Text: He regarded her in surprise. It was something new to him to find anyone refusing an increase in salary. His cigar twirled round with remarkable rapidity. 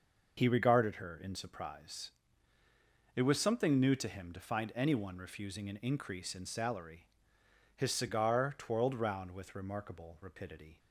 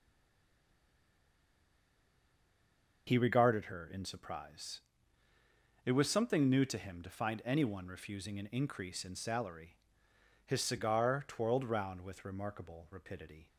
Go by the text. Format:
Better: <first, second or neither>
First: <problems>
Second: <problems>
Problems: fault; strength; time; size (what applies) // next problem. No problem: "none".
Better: first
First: none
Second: stays silent before the first word; strong; until 3.0 s; 3.0 s long